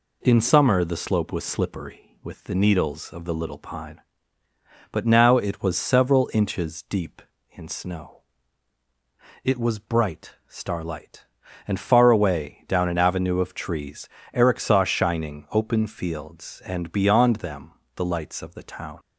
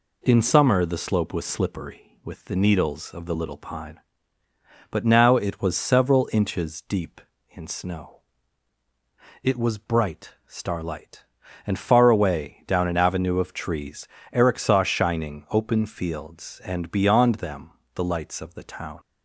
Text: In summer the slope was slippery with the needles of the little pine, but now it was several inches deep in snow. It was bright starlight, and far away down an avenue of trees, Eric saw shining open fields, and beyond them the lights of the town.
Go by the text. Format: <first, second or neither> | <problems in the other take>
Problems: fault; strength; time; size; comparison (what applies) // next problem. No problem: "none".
neither | pauses between "them" and "the"; slight; the same in both